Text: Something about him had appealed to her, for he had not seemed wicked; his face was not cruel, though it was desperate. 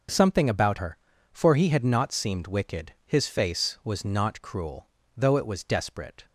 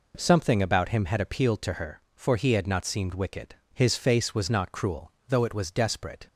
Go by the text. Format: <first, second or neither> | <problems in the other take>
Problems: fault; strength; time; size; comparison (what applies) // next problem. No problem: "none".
second | skips "him had appealed to"; at 0.7 s